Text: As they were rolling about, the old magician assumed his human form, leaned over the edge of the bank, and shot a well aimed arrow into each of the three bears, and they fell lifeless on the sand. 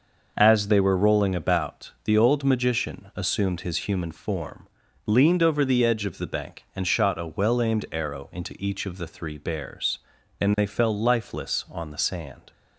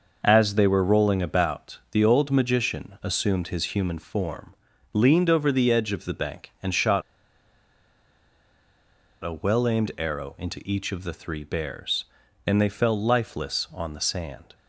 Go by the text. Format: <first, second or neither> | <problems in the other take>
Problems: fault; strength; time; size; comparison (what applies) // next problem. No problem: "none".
first | pauses between "shot" and "a"; strong; at 7.0 s; 2.2 s long